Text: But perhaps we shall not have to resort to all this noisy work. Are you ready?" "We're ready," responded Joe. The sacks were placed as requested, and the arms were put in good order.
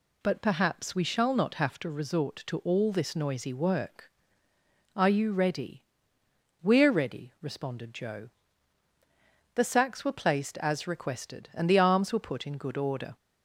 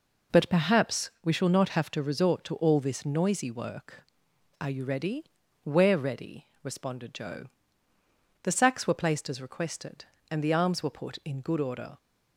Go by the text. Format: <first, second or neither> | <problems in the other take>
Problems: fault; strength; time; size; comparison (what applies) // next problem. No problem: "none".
neither | none